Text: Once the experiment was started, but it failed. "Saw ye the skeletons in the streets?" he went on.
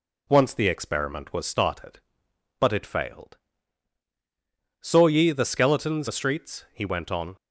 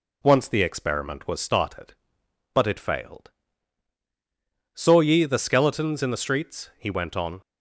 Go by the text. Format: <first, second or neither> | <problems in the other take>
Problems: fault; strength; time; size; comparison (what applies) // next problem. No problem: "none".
second | skips "in"; at 6.0 s